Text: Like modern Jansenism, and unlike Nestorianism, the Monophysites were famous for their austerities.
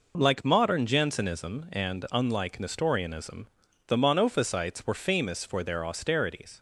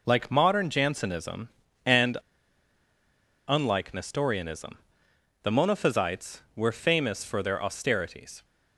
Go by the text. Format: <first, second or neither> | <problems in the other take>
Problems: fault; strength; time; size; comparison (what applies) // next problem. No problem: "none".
first | pauses between "and" and "unlike"; strong; at 2.1 s; 1.3 s long